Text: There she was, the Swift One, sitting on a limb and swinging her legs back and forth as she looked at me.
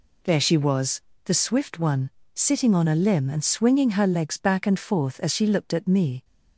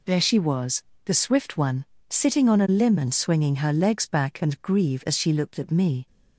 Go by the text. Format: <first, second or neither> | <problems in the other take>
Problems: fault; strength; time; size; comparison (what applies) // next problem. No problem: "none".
first | says "grieve" for "forth"; at 4.6 s